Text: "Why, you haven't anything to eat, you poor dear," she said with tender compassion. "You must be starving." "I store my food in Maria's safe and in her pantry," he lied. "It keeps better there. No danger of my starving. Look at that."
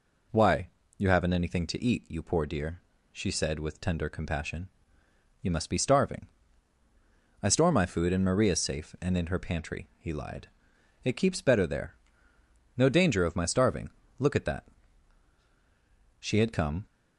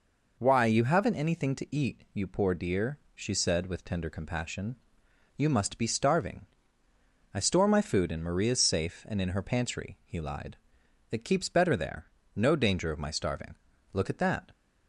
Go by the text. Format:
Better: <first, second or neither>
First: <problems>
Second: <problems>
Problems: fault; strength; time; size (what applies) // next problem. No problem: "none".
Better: second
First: goes on to say "She had come"; noticeable; from 16.1 s on; 0.66 s long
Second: none